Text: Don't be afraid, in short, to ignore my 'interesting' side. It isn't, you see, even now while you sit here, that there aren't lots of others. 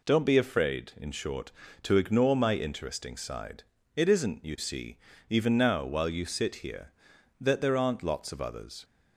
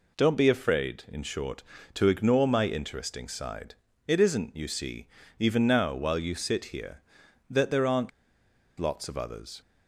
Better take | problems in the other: first | pauses between "aren't" and "lots"; noticeable; at 8.1 s; 0.68 s long

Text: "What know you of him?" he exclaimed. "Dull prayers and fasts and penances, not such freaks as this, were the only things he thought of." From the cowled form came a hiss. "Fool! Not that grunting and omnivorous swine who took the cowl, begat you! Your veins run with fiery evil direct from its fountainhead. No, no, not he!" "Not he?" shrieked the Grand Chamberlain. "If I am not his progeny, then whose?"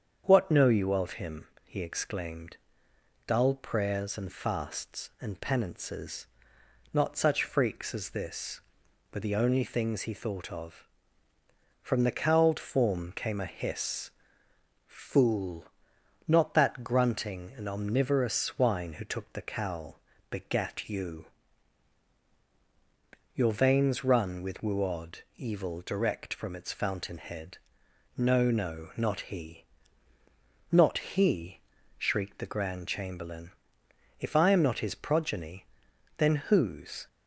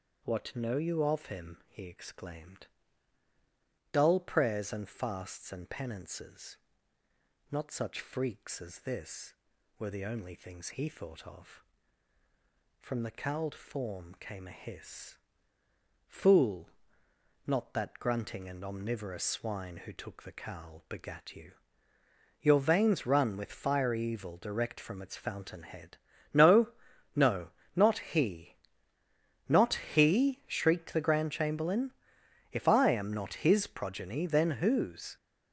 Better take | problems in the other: second | starts louder than the rest; strong; until 1.2 s; 7.5 dB; also in the second // says "wuod" for "fiery"; at 24.6 s

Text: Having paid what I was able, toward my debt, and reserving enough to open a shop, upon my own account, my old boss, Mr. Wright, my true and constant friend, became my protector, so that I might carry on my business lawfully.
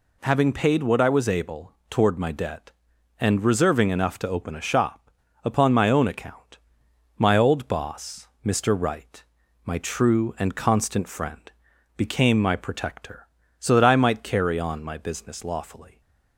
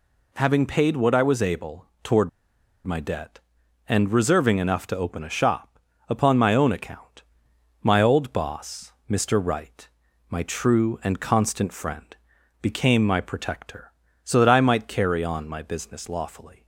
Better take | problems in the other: first | pauses between "toward" and "my"; noticeable; at 2.2 s; 0.57 s long

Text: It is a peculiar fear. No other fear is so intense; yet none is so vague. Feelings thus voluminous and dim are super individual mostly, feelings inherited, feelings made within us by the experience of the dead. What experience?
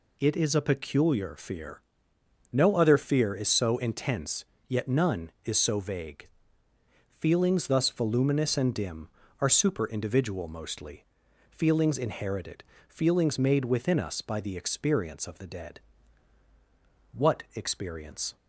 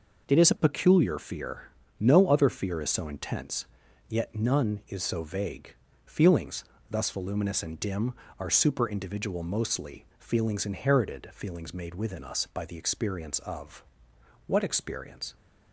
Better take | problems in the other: first | pauses between "Feelings" and "thus"; slight; at 6.6 s; 0.26 s long // skips "the dead"; at 14.1 s

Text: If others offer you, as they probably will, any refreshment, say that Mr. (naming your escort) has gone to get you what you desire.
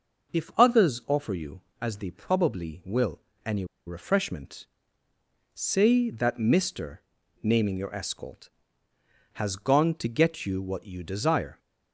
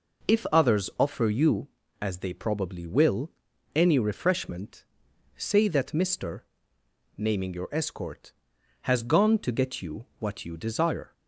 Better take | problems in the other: second | pauses between "any" and "refreshment"; slight; at 3.6 s; 0.21 s long

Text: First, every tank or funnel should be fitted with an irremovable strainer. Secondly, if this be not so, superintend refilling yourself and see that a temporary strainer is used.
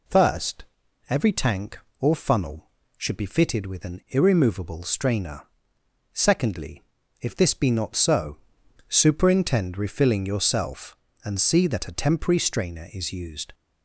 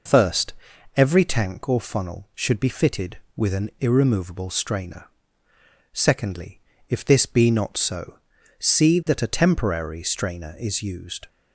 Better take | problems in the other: first | skips "superintend refilling yourself and"; at 8.3 s

